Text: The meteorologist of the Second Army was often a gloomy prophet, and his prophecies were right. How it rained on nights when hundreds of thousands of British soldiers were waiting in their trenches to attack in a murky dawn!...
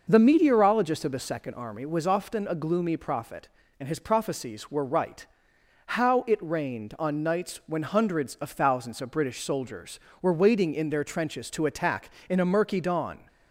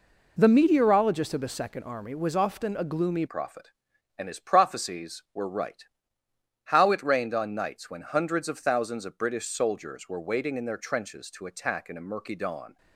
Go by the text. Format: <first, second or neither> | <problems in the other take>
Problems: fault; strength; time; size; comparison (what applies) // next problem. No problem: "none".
first | changes voice at "prophet"; from 3.2 s on; 9.5 s long